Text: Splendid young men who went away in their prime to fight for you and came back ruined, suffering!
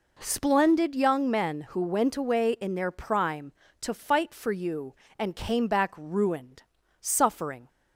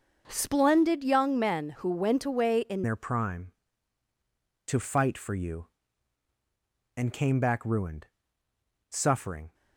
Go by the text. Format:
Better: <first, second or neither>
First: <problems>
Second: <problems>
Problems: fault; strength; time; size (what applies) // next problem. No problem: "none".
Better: first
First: none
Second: starts louder than the rest; until 1.2 s; 6.5 dB // changes voice at "their"; from 2.8 s on; 6.7 s long